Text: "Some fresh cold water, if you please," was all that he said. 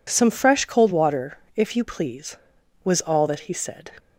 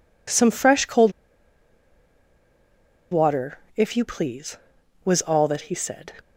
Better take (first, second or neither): first